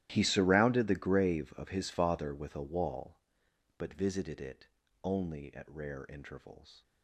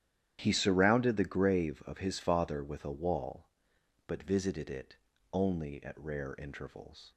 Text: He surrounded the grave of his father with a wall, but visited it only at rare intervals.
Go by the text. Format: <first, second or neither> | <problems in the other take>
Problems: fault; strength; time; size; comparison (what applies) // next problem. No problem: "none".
second | gets quieter; strong; throughout; 20 dB // starts louder than the rest; strong; until 1.1 s; 13.5 dB; strong in the second // pauses between "it" and "only"; at 4.6 s; 0.38 s long; also in the second